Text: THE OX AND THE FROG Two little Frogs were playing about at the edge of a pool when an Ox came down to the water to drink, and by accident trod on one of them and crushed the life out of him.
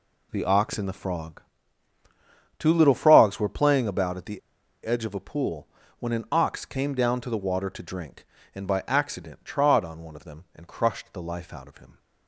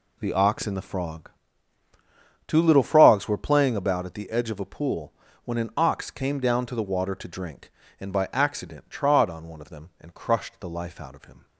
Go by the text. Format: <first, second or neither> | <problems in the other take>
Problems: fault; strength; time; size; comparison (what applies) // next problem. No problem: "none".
second | pauses between "FROG" and "Two"; at 1.4 s; 1.1 s long; also in the second // pauses between "the" and "edge"; noticeable; at 4.3 s; 0.47 s long // pauses between "pool" and "when"; slight; at 5.6 s; 0.32 s long; slight in the second